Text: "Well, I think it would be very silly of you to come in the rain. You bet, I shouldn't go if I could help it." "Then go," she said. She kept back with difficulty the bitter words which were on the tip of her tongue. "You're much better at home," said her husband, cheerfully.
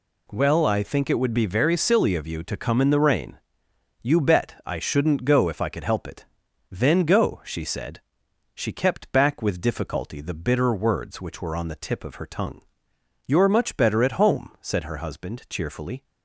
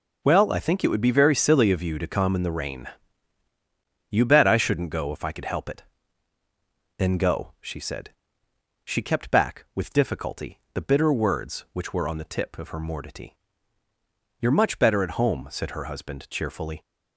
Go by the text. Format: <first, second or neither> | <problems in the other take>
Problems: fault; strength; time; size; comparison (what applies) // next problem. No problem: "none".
first | says "mortity" for "tongue"; at 12.7 s